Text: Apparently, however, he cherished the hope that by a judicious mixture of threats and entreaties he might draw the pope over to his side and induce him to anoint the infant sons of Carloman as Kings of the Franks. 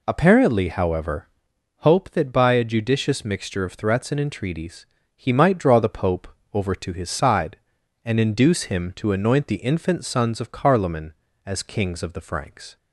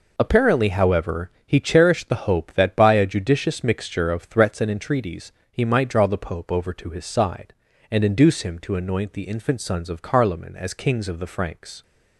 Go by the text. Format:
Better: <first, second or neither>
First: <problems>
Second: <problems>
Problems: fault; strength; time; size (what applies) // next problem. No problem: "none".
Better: second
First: skips "he cherished the"; at 1.5 s // pauses between "entreaties" and "he"; slight; at 4.8 s; 0.30 s long // pauses between "pope" and "over"; slight; at 6.2 s; 0.26 s long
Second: pauses between "entreaties" and "he"; slight; at 5.3 s; 0.20 s long